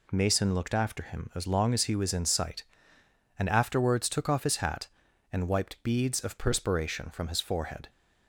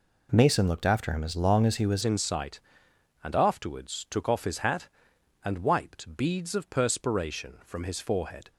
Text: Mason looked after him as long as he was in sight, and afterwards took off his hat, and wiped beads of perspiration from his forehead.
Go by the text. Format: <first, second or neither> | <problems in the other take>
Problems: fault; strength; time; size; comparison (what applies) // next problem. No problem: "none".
first | changes voice at "in"; from 2.0 s on; 6.5 s long